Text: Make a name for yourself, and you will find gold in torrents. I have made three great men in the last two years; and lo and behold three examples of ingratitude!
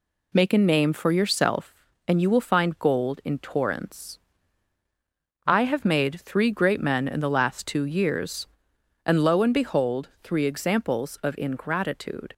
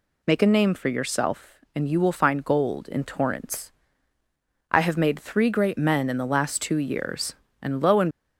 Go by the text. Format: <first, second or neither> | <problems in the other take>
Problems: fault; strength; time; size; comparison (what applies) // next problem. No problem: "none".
first | stops before "behold three examples of ingratitude"; at 8.1 s